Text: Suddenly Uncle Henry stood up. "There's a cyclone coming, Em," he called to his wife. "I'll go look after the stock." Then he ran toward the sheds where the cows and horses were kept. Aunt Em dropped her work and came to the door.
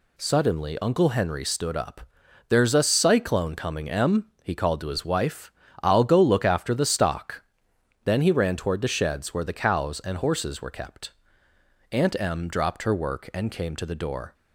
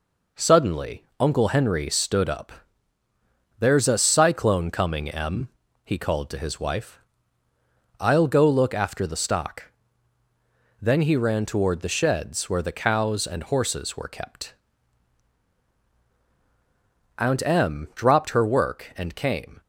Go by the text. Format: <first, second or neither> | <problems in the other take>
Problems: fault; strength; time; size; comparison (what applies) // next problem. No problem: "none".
first | pauses between "Suddenly" and "Uncle"; slight; at 1.0 s; 0.16 s long // stops before "to the door"; at 19.6 s